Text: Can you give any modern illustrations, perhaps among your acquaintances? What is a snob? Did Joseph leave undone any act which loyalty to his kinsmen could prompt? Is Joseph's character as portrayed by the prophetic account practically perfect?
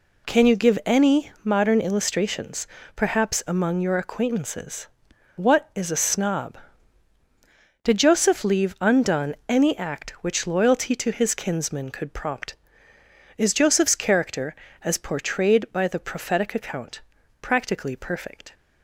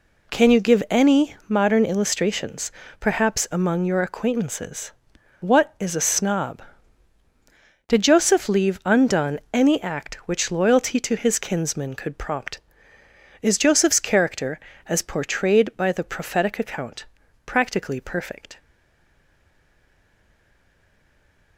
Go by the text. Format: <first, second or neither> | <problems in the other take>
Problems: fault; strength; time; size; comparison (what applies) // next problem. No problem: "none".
first | pauses between "account" and "practically"; at 17.0 s; 0.40 s long; also in the first // stays silent after the last word; strong; from 18.5 s on; 3.0 s long